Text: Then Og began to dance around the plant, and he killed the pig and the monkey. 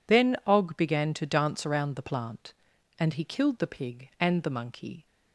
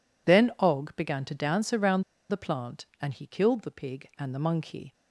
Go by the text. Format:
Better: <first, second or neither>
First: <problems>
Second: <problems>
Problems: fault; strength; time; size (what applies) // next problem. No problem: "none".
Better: first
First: none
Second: pauses between "around" and "the"; slight; at 2.0 s; 0.29 s long